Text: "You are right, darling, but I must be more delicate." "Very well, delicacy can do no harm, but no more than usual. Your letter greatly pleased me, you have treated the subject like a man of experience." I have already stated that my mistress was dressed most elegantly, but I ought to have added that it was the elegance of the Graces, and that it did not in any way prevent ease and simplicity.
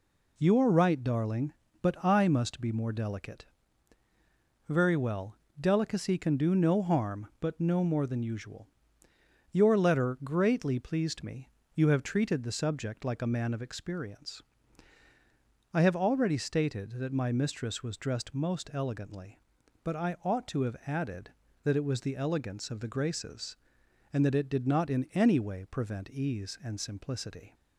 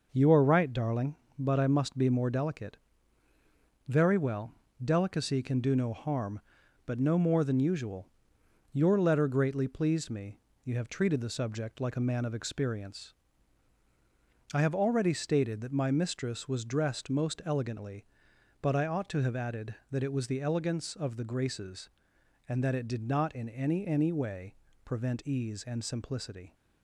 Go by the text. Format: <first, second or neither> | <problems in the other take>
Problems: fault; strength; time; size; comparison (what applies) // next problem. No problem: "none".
first | says "any" twice; at 23.8 s // pauses between "way" and "prevent"; slight; at 24.5 s; 0.30 s long